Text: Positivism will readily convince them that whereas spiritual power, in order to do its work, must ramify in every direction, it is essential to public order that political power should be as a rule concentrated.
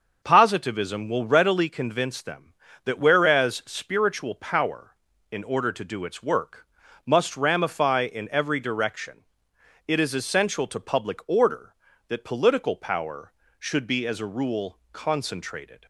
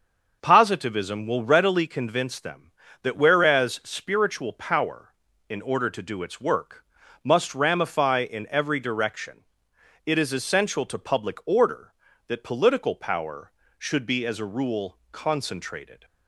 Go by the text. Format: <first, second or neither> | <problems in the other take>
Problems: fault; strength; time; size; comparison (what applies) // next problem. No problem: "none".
neither | starts louder than the rest; the same in both